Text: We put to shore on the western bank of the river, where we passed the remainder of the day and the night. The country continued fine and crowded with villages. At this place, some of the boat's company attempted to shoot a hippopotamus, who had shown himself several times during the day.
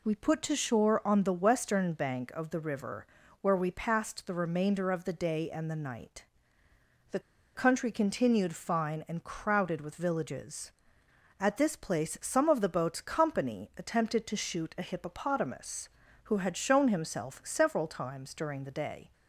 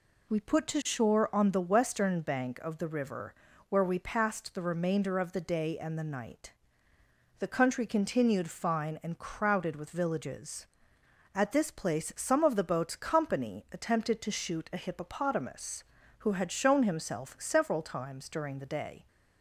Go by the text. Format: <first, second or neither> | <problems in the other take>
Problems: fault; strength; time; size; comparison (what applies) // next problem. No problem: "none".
second | pauses between "The" and "country"; slight; at 7.1 s; 0.36 s long